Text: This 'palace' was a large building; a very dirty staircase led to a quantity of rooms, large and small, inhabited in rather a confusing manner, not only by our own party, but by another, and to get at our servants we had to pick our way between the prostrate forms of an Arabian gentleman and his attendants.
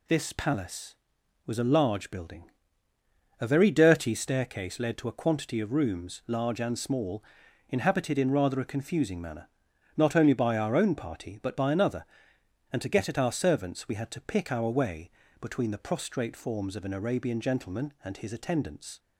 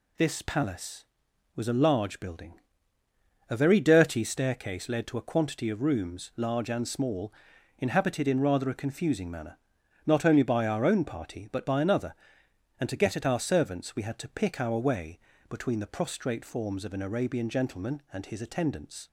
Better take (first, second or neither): neither